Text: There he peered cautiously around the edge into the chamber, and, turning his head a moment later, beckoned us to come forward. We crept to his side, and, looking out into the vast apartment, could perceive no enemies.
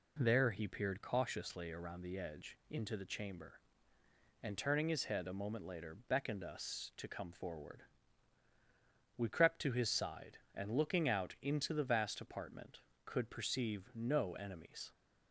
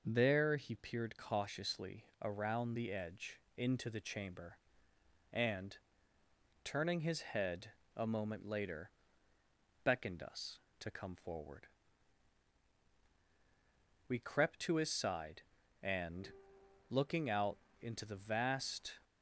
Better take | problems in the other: first | pauses between "cautiously" and "around"; slight; at 2.0 s; 0.18 s long // pauses between "edge" and "into"; slight; at 3.3 s; 0.16 s long // pauses between "head" and "a"; slight; at 7.6 s; 0.26 s long // pauses between "out" and "into"; slight; at 17.5 s; 0.22 s long // stops before "apartment could perceive no enemies"; at 19.0 s

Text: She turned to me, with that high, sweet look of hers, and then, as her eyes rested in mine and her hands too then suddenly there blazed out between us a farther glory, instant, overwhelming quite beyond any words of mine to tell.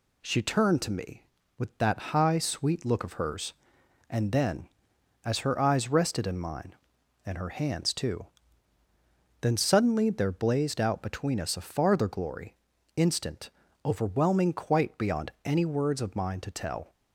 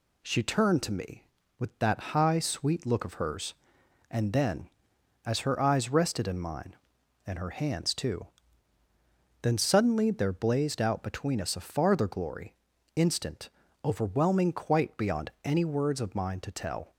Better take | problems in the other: neither | pauses between "too" and "then"; the same in both

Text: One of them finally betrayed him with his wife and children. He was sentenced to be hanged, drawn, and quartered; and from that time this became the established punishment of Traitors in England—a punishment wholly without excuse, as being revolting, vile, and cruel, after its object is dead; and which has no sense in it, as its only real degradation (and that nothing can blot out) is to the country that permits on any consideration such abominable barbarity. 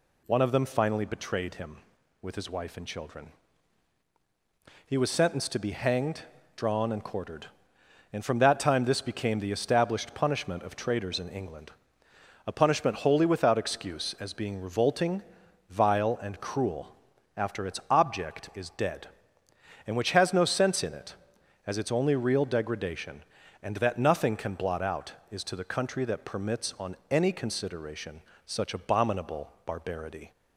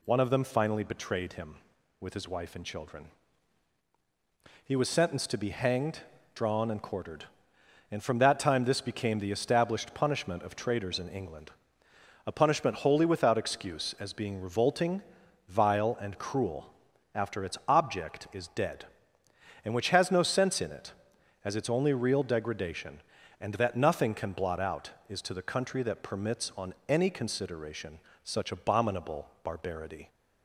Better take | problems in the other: neither | pauses between "on" and "any"; slight; the same in both // pauses between "consideration" and "such"; slight; the same in both

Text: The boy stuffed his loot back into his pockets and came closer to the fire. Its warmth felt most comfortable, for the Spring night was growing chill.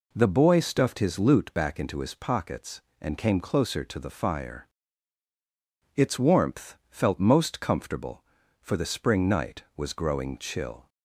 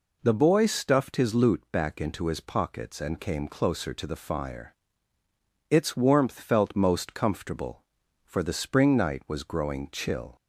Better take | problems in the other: neither | none

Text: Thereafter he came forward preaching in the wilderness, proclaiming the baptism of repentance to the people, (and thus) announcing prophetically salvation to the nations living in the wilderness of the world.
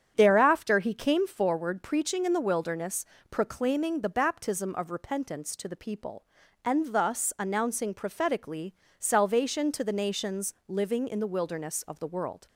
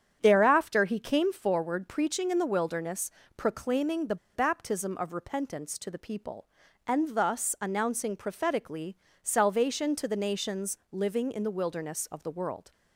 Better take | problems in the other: first | starts louder than the rest; strong; until 1.2 s; 8.5 dB; strong in the first // pauses between "the" and "baptism"; slight; at 4.1 s; 0.19 s long // pauses between "prophetically" and "salvation"; slight; at 8.9 s; 0.24 s long; slight in the first

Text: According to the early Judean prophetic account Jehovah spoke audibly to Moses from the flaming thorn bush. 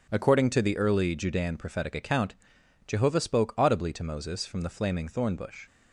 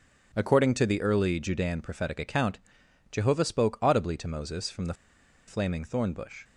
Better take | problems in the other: first | starts louder than the rest; strong; until 1.3 s; 8 dB // pauses between "account" and "Jehovah"; noticeable; at 2.5 s; 0.52 s long; noticeable in the first // pauses between "the" and "flaming"; noticeable; at 4.9 s; 0.52 s long

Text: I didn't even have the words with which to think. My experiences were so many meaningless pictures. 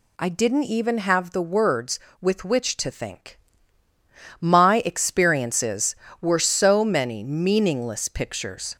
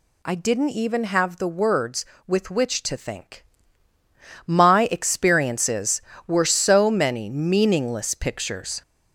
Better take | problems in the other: first | gets louder; noticeable; throughout; 4.5 dB

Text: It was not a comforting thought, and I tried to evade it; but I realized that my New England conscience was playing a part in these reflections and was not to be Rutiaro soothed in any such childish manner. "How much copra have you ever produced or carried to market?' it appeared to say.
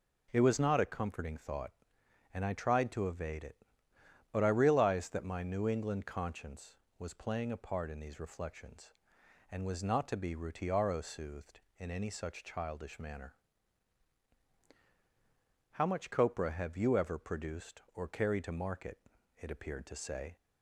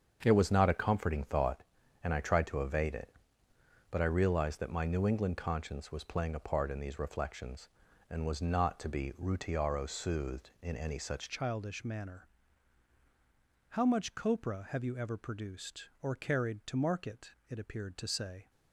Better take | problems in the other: first | starts louder than the rest; strong; until 1.2 s; 7.5 dB // changes voice at "childish"; from 11.2 s on; 7.2 s long

